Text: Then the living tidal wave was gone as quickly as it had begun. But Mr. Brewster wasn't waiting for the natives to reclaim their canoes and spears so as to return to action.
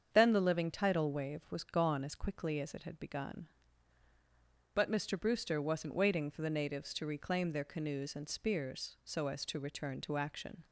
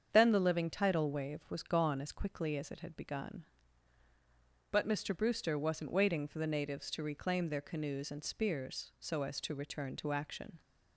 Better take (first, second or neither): neither